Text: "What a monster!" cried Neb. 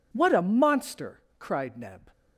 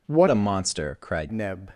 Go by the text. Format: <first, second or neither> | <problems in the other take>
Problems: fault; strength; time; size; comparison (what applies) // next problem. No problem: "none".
first | changes voice from "a" to "cried"; from 0.2 to 1.2 s; 1.0 s long